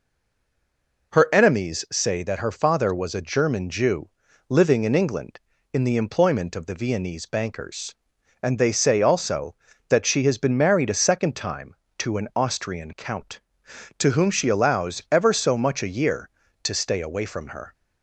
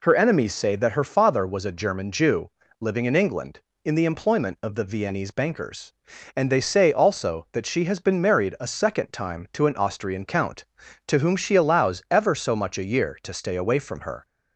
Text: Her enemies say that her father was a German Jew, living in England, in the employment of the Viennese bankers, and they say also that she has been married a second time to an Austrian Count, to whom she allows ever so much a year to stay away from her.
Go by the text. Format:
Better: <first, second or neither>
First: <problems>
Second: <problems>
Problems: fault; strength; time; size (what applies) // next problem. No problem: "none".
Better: second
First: stays silent before the first word; until 1.1 s; 1.1 s long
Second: none